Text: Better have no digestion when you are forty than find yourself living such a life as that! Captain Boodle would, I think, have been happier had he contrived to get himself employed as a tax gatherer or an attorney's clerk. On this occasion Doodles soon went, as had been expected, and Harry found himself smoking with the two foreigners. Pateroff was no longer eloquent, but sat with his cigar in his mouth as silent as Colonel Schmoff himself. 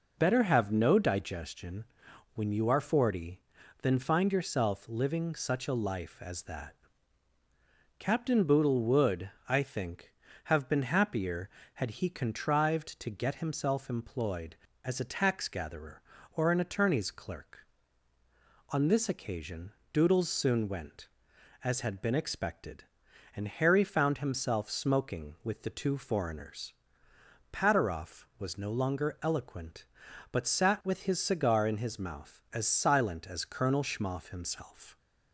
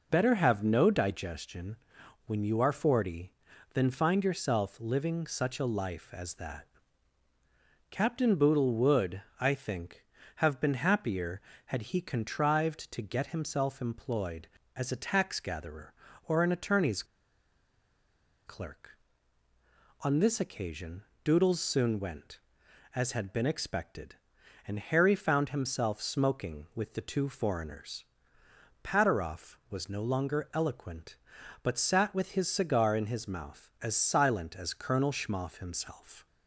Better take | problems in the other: first | pauses between "digestion" and "when"; noticeable; at 1.7 s; 0.50 s long; noticeable in the first // pauses between "attorney's" and "clerk"; strong; at 17.0 s; 1.4 s long // pauses between "occasion" and "Doodles"; slight; at 21.0 s; 0.22 s long; slight in the first

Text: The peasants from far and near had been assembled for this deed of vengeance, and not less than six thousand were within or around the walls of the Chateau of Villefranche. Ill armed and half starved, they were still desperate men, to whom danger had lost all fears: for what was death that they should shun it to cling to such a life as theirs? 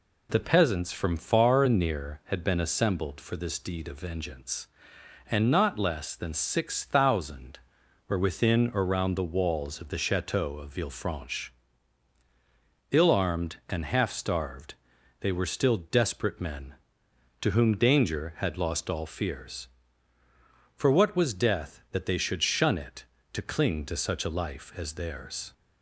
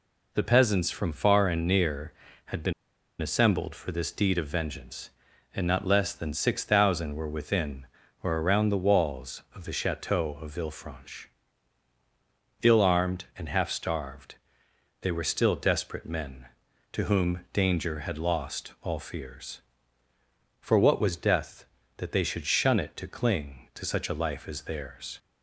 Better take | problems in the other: first | pauses between "been" and "assembled"; noticeable; at 2.7 s; 0.49 s long

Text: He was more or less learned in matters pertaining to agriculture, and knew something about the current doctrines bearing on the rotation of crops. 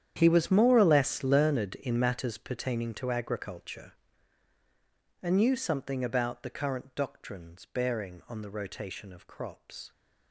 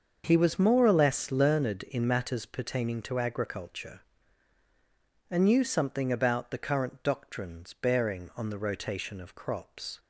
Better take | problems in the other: second | gets quieter; strong; throughout; 17 dB // starts louder than the rest; strong; until 1.1 s; 9.5 dB; also in the second

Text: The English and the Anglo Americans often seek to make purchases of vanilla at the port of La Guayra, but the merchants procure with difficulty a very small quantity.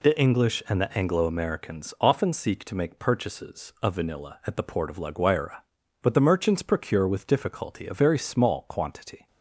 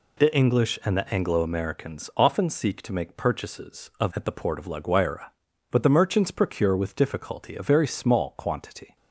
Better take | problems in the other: first | skips "vanilla"; at 4.1 s

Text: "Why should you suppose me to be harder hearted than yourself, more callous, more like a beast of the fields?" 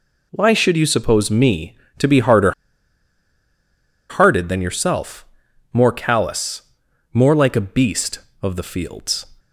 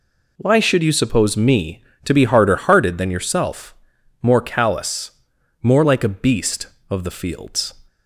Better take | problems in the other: second | pauses between "harder" and "hearted"; strong; at 2.5 s; 1.5 s long

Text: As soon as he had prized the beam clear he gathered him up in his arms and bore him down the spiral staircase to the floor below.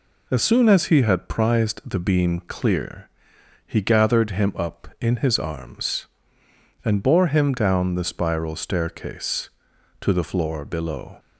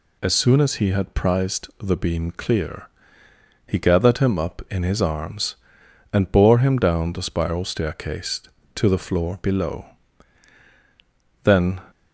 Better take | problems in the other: first | pauses between "clear" and "he"; noticeable; at 2.8 s; 0.78 s long; noticeable in the first // goes on to say "Then"; slight; from 11.4 s on; 0.38 s long

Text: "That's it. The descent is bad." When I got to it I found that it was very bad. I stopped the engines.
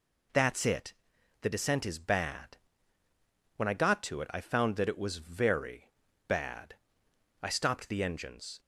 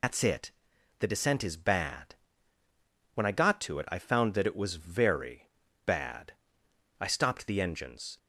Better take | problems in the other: first | loses the start of "That's"; at 0.0 s; 140 ms // pauses between "very" and "bad"; at 5.4 s; 0.38 s long; also in the first

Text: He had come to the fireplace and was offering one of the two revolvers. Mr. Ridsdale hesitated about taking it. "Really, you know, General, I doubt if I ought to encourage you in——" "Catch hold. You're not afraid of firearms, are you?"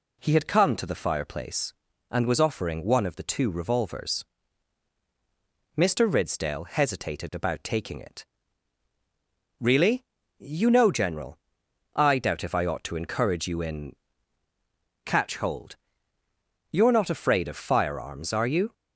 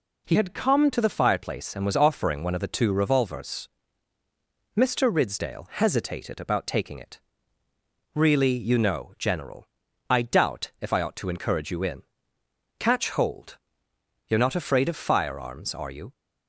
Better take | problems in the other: first | changes voice from "had" to "come"; from 0.3 to 0.9 s; 0.6 s long

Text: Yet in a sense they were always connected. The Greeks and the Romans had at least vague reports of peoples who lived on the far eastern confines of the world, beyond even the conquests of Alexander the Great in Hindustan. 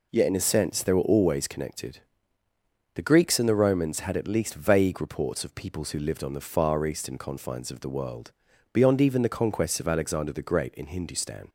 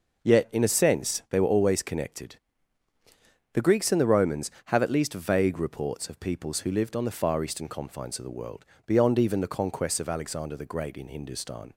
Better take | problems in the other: first | says "have" for "had"; at 4.6 s

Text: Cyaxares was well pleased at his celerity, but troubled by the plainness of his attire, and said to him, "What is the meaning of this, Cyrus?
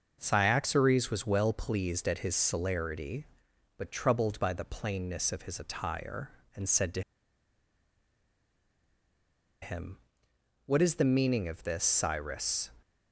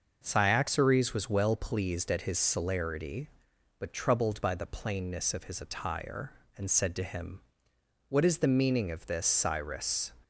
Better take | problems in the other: second | starts louder than the rest; noticeable; until 1.2 s; 6 dB; noticeable in the second // pauses between "to" and "him"; strong; at 7.0 s; 2.6 s long

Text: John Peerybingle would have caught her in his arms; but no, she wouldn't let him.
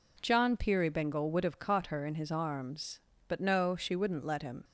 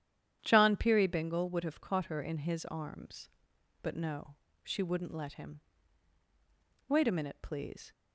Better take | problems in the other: first | starts louder than the rest; strong; until 1.4 s; 10 dB // goes on to say "Wait a minute please"; noticeable; from 6.8 s on; 1.0 s long

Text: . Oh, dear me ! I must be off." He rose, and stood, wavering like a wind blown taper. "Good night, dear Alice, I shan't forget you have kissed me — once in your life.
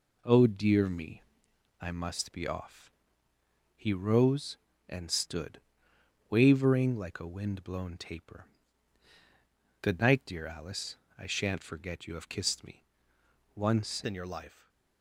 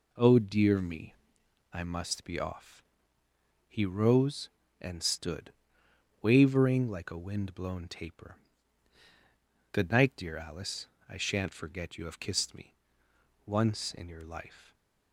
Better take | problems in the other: second | changes voice at "in"; from 14.0 s on; 0.6 s long // stays silent after the last word; slight; from 14.4 s on; 0.6 s long; slight in the second

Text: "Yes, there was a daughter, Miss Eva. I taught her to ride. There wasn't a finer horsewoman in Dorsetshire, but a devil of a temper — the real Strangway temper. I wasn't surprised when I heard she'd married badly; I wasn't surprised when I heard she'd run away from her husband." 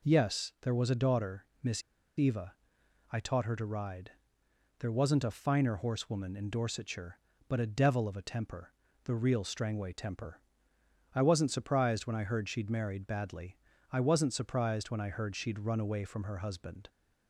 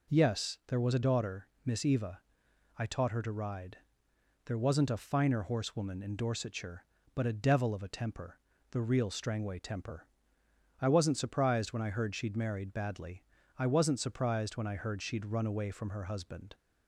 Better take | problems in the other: second | pauses between "Miss" and "Eva"; at 1.8 s; 0.36 s long

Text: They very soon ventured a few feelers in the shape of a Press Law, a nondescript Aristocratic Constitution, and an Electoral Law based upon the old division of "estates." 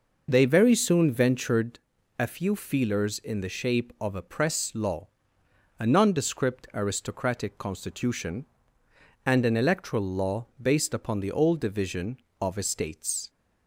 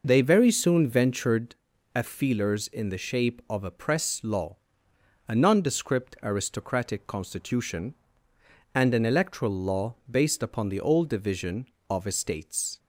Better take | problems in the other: first | pauses between "ventured" and "a"; at 1.5 s; 0.40 s long; also in the first // skips "few"; at 2.0 s // pauses between "Law" and "based"; slight; at 9.9 s; 0.18 s long; slight in the first

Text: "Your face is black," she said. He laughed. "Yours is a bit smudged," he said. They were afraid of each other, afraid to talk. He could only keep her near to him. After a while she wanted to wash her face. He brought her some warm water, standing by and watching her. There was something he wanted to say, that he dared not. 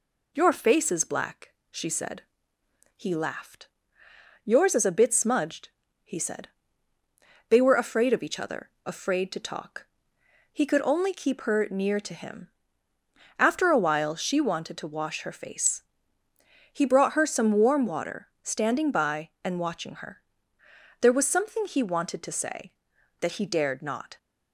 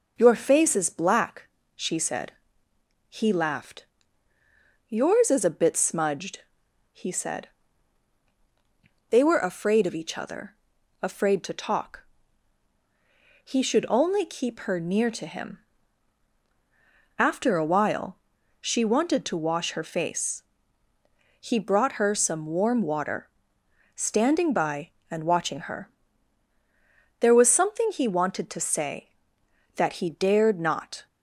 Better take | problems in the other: first | says "should" for "could"; at 13.6 s // pauses between "while" and "she"; at 18.1 s; 0.42 s long

